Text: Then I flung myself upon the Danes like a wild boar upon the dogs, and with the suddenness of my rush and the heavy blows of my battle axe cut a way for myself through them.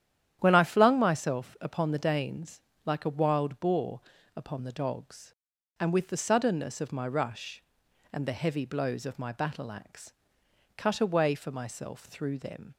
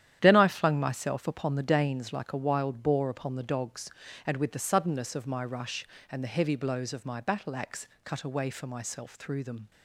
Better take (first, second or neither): second